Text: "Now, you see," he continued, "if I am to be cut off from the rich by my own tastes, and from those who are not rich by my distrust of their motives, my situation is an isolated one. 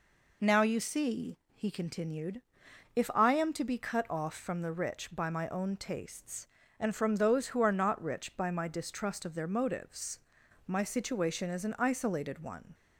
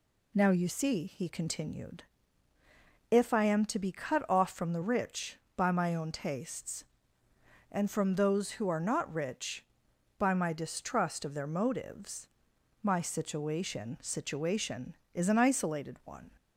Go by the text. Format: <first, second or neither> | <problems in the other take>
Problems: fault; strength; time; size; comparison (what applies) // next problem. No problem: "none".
first | says "situation" twice; at 14.0 s